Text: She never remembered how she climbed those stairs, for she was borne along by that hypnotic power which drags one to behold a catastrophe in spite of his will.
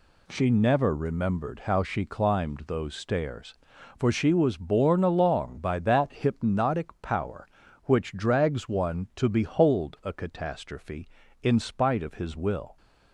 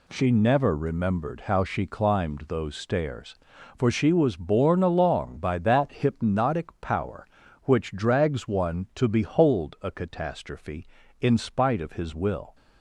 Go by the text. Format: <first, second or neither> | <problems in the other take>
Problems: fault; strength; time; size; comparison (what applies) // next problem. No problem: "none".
neither | none